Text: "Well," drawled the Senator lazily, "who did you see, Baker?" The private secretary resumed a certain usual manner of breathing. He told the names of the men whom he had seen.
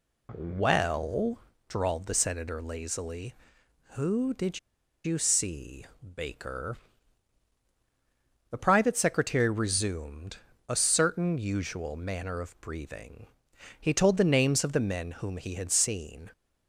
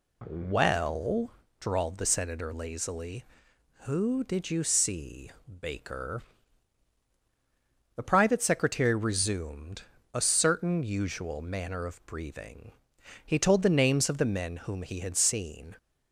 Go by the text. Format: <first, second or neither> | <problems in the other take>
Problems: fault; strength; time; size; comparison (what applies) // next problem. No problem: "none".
second | pauses between "did" and "you"; at 4.5 s; 0.45 s long // pauses between "resumed" and "a"; slight; at 10.3 s; 0.28 s long; slight in the second